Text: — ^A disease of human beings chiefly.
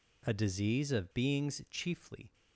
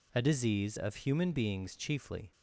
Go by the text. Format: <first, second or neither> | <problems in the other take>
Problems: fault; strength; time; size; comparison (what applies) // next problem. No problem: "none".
second | skips "human"; at 1.1 s